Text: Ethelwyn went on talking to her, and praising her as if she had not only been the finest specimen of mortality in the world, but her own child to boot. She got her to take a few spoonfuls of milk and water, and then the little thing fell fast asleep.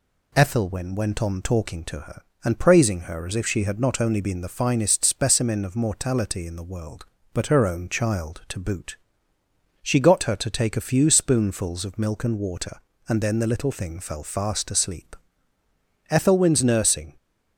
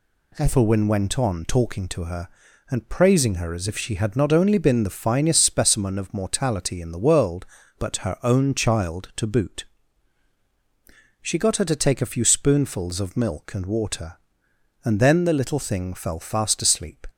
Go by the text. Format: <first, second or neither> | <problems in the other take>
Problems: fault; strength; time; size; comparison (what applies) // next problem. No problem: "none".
second | goes on to say "Ethelwyn's nursing"; noticeable; from 16.1 s on; 1.0 s long